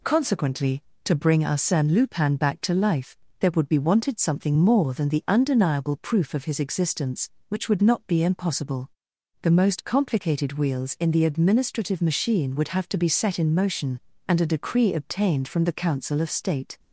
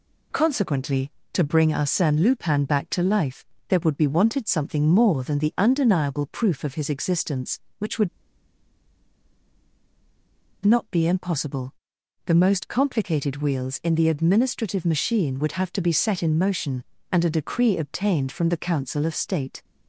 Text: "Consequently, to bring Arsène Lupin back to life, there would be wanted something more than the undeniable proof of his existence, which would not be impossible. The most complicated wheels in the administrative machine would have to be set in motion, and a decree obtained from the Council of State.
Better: first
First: none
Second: pauses between "would" and "not"; strong; at 8.0 s; 2.5 s long

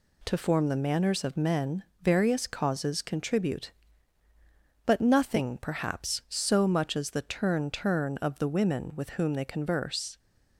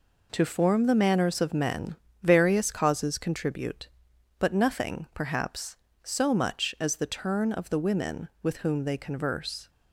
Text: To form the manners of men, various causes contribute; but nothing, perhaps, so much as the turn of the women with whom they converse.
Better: second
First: says "turn" twice; at 7.7 s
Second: none

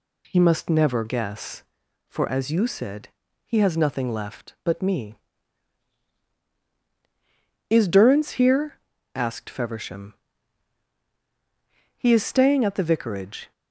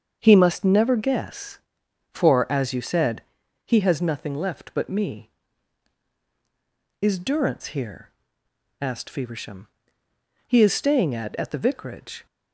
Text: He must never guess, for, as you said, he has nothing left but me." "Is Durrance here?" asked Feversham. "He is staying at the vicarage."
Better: first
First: none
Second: starts louder than the rest; until 1.2 s; 7 dB // says "at" twice; at 11.3 s

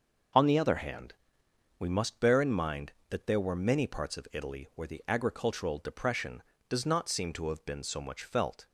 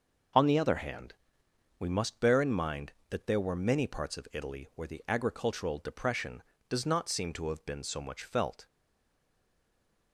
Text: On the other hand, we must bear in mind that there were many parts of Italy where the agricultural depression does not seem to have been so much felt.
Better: first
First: none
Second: stays silent after the last word; noticeable; from 8.6 s on; 1.5 s long

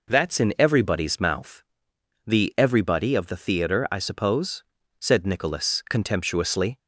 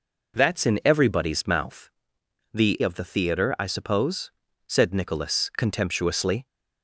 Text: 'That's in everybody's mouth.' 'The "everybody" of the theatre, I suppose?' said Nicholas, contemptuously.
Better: first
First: none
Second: skips "everybody"; at 2.8 s

